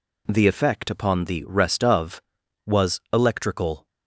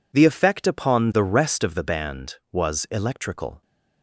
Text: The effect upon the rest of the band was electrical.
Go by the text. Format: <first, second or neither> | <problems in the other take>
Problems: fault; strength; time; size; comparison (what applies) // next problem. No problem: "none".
second | skips "the band"; at 2.4 s